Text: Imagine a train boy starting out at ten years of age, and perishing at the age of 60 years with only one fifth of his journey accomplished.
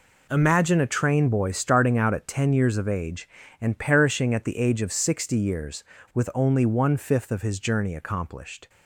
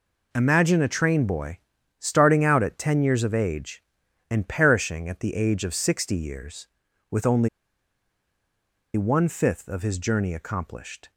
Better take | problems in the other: first | pauses between "boy" and "starting"; at 1.5 s; 0.40 s long // pauses between "only" and "one"; strong; at 7.4 s; 1.4 s long

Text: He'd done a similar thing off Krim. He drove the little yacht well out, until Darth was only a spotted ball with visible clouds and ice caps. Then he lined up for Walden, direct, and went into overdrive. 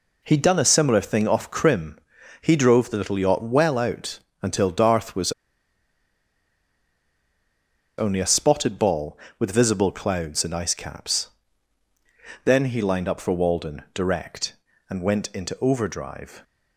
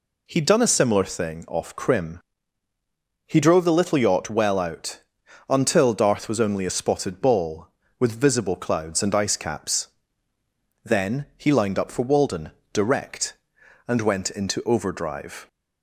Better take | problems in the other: second | pauses between "was" and "only"; strong; at 5.3 s; 2.6 s long

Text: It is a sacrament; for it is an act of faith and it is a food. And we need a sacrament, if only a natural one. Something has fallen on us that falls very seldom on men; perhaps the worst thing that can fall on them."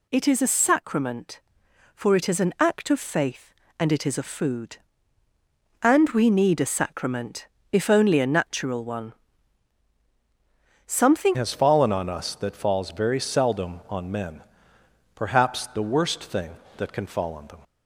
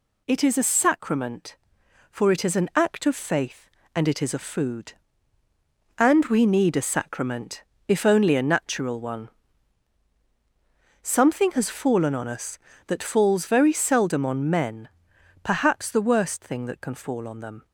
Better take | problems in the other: second | changes voice at "has"; from 11.3 s on; 6.3 s long

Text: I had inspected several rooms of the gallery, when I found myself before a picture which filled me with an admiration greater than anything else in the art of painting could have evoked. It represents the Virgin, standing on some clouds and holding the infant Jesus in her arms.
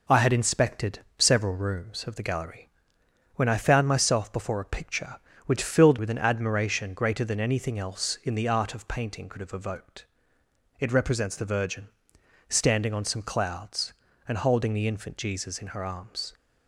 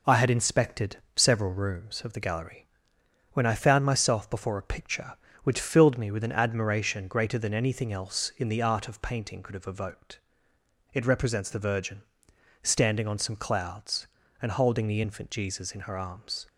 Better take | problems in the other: second | pauses between "inspected" and "several"; slight; at 0.9 s; 0.18 s long; slight in the second // skips "me"; at 5.9 s

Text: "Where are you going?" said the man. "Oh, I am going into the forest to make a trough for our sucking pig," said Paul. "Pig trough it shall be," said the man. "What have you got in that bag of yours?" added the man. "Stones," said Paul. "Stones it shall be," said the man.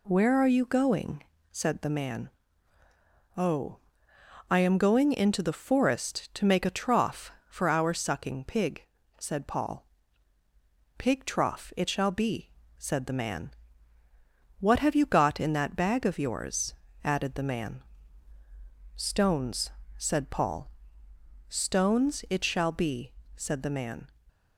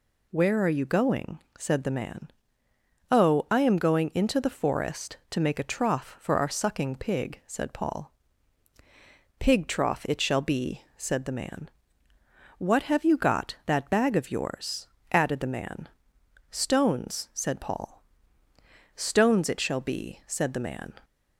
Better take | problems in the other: first | skips "in"; at 13.6 s

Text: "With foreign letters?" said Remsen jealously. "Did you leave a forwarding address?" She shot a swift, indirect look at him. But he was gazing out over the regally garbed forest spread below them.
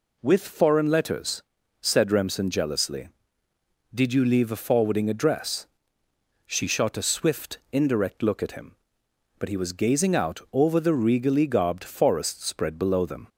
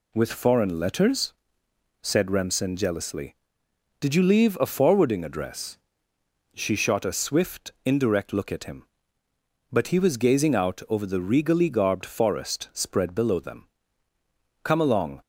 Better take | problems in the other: first | goes on to say "Come along"; from 14.6 s on; 0.58 s long

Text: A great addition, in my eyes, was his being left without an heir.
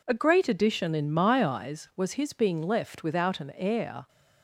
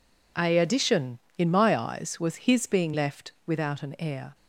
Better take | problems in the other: first | skips "great"; at 0.5 s // pauses between "left" and "without"; slight; at 3.3 s; 0.16 s long

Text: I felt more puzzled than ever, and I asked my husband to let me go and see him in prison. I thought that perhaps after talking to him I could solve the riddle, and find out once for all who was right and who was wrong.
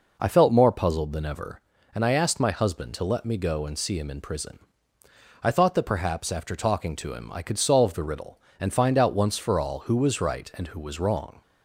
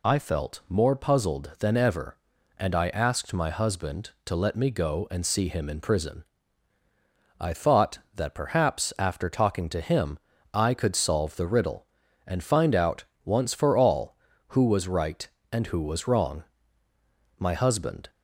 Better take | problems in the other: first | pauses between "him" and "I"; slight; at 10.1 s; 0.36 s long // pauses between "out" and "once"; slight; at 13.0 s; 0.20 s long // goes on to say "My husband"; noticeable; from 17.3 s on; 0.72 s long

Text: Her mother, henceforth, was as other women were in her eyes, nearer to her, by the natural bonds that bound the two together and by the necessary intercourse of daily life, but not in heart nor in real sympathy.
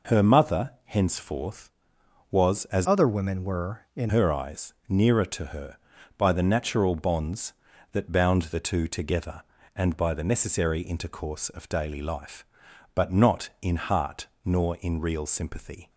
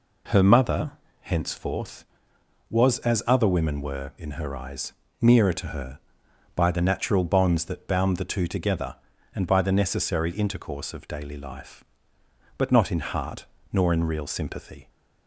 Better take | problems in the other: second | changes voice from "other" to "in"; from 2.8 to 4.0 s; 1.2 s long // pauses between "heart" and "nor"; slight; at 14.2 s; 0.16 s long; slight in the second

